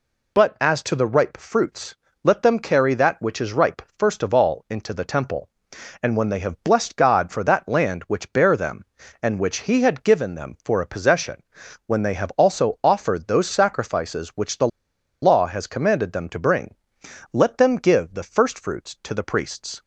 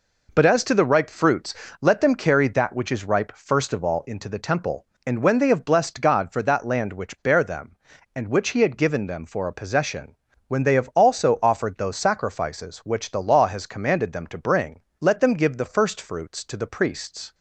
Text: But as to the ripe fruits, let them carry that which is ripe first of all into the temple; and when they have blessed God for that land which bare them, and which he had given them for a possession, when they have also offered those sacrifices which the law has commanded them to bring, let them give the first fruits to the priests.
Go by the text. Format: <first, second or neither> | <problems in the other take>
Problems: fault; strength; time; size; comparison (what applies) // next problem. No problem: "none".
second | pauses between "ripe" and "first"; slight; at 3.8 s; 0.16 s long // pauses between "the" and "law"; noticeable; at 14.6 s; 0.55 s long